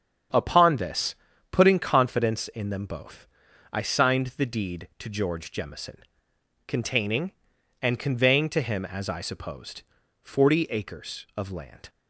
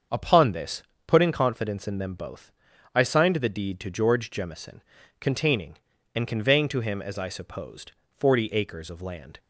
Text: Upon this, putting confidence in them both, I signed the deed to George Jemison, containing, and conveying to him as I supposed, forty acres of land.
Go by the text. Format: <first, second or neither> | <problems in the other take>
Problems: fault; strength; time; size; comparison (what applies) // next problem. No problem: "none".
neither | starts louder than the rest; the same in both